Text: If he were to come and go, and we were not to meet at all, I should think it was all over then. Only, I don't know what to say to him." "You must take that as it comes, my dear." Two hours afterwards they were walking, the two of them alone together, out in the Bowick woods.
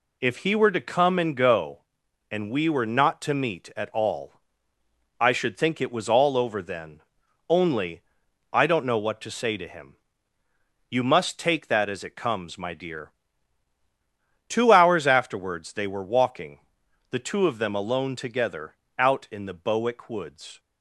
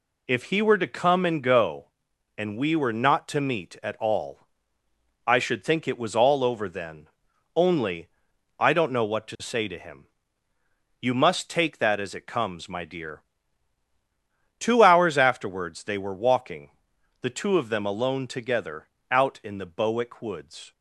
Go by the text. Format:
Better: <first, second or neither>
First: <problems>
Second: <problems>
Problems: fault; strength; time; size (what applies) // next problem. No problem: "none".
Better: neither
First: none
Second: none